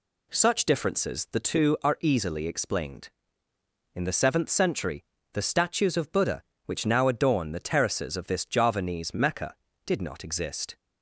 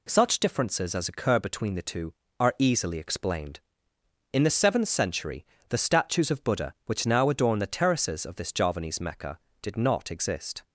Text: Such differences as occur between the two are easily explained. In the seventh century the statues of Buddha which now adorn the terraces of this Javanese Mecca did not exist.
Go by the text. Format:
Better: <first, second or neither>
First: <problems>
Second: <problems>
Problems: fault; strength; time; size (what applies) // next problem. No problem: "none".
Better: second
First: skips "as occur between"; at 1.2 s // pauses between "century" and "the"; slight; at 5.0 s; 0.30 s long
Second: pauses between "century" and "the"; slight; at 5.4 s; 0.26 s long